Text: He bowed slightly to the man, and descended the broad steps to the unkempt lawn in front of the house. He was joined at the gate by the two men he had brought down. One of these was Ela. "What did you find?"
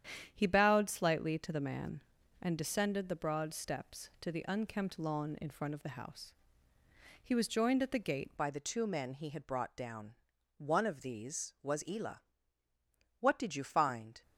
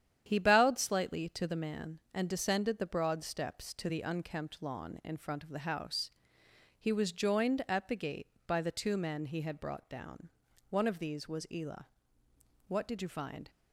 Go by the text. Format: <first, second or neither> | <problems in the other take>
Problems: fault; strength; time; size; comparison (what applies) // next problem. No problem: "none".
second | starts louder than the rest; strong; until 1.3 s; 9.5 dB; strong in the second // changes voice at "by"; from 8.3 s on; 5.9 s long